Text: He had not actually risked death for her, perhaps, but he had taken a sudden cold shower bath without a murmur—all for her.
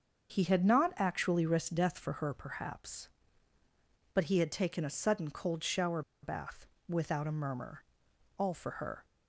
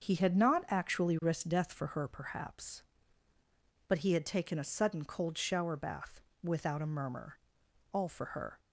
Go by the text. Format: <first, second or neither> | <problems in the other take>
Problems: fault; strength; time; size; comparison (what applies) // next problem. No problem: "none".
second | starts louder than the rest; until 1.3 s; 6.5 dB; also in the second // pauses between "shower" and "bath"; slight; at 6.0 s; 0.22 s long // pauses between "bath" and "without"; slight; at 6.6 s; 0.22 s long; slight in the second